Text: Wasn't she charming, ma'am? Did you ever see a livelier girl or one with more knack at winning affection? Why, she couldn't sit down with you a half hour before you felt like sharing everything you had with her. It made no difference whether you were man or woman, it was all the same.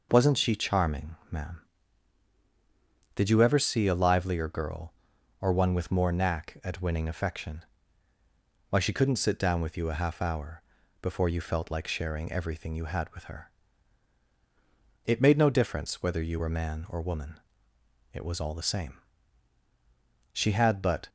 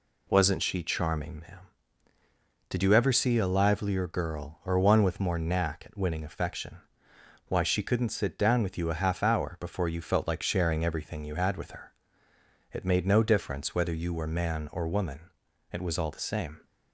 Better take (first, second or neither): second